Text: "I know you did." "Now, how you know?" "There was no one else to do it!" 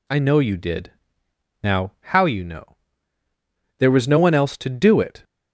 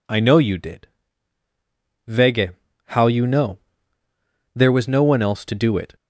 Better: first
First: none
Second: says "Vege" for "Now"; at 2.0 s

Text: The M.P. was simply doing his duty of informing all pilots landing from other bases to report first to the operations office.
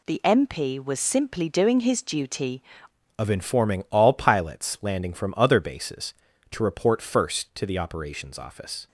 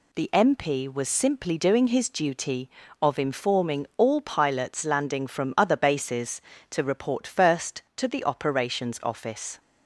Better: second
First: changes voice at "of"; from 3.1 s on; 5.7 s long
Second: none

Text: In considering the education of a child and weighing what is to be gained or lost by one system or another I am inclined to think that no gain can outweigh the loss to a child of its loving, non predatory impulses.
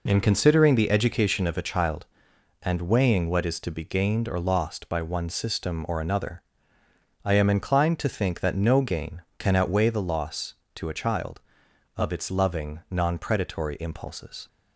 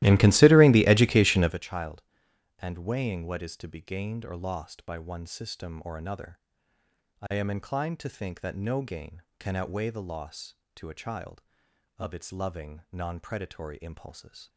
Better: first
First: pauses between "another" and "I"; noticeable; at 6.4 s; 0.82 s long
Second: starts louder than the rest; strong; until 1.6 s; 16.5 dB // pauses between "another" and "I"; noticeable; at 6.3 s; 0.82 s long

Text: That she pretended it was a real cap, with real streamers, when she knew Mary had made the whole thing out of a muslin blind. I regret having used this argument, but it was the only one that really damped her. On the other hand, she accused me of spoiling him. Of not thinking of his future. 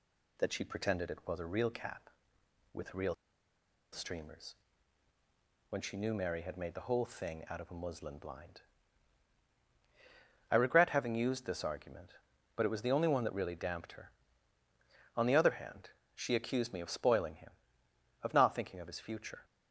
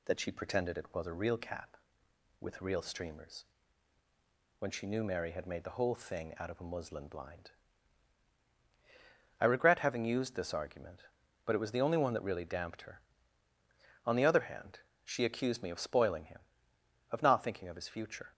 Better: second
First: pauses between "real" and "streamers"; noticeable; at 3.1 s; 0.77 s long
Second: none

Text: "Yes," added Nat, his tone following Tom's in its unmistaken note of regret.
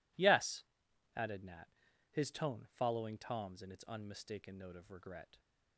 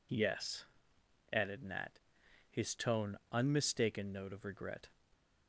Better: first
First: none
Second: skips "following Tom's in its"; at 3.2 s

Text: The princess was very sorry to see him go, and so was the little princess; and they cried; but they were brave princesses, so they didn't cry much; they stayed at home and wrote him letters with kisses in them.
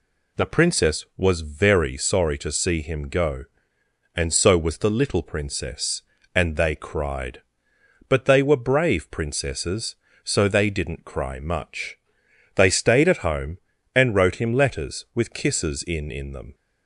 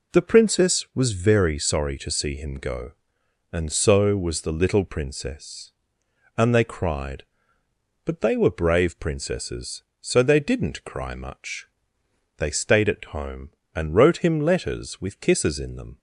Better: second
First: says "in" twice; at 16.1 s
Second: none

